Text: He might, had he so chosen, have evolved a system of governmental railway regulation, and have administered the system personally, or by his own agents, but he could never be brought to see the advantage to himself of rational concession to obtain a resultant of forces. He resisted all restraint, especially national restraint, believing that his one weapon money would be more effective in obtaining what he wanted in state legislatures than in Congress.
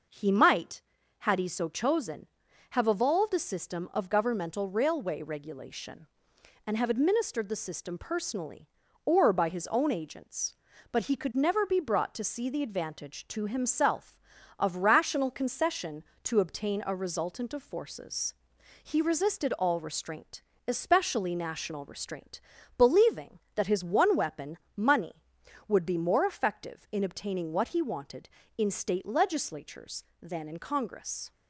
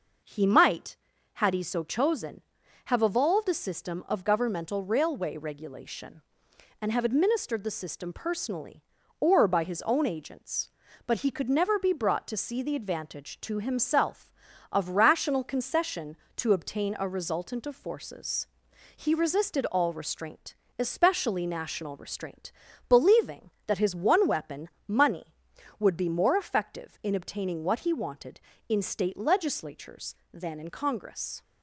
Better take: neither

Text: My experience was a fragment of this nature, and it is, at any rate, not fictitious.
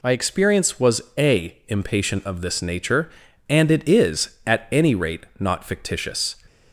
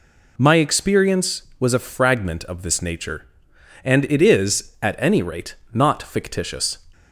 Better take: second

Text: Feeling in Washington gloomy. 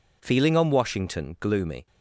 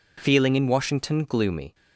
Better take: second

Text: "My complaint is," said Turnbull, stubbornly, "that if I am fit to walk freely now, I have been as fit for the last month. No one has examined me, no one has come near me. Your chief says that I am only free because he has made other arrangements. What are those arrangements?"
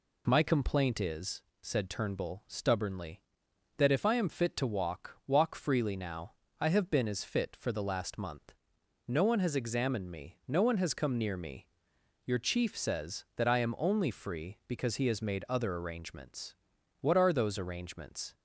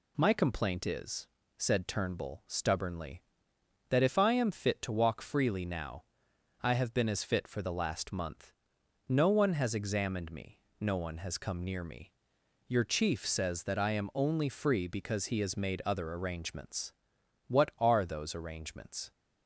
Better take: second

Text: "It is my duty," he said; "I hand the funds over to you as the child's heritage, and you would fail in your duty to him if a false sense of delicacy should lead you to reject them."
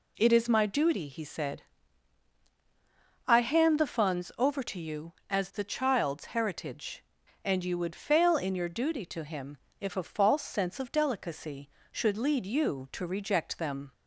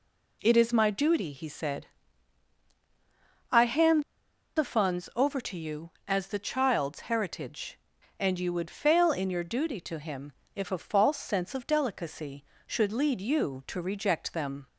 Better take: first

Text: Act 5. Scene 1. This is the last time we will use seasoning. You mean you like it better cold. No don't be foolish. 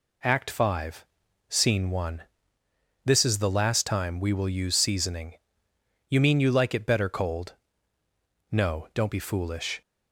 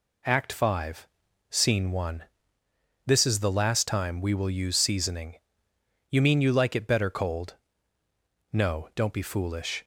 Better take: neither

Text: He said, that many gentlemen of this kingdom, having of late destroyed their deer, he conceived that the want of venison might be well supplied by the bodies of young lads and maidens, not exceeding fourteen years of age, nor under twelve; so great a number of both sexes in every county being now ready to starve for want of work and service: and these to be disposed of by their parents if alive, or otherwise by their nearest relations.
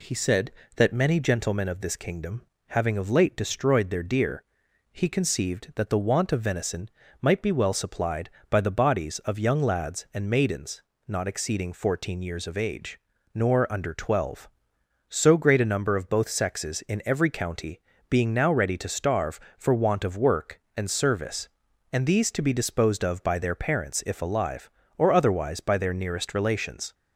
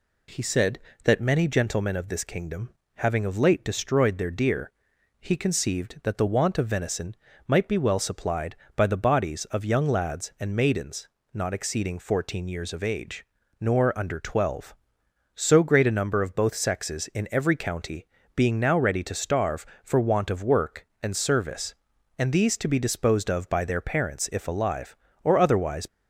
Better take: first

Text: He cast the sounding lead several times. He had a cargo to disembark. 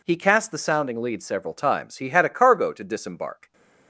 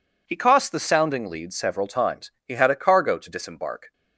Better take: first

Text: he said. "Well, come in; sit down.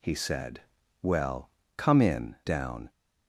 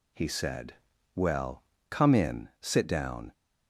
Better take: second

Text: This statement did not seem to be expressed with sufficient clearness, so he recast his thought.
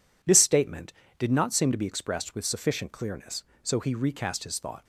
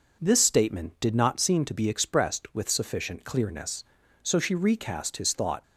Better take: first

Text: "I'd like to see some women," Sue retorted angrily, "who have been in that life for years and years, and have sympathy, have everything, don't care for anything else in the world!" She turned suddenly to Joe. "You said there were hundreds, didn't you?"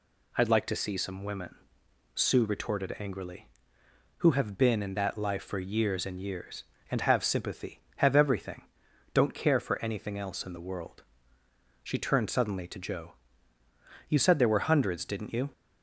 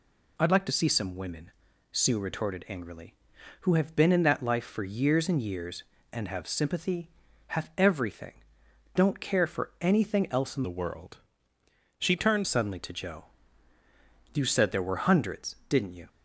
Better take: first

